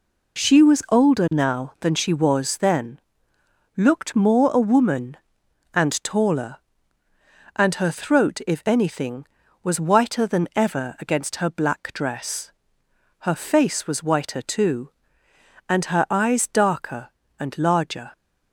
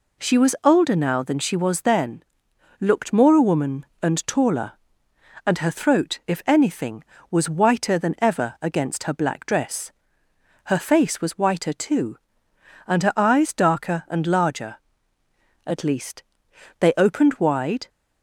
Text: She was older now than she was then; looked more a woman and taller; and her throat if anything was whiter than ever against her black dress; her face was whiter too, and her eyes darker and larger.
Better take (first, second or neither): first